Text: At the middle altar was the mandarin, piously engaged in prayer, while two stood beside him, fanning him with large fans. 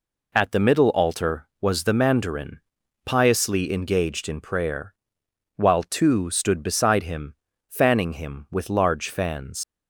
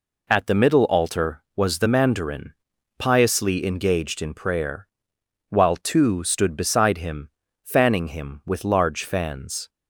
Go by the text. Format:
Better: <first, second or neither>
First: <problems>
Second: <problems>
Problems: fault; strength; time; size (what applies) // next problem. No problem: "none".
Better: second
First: leaves "fans" unfinished; at 9.6 s; 115 ms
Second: none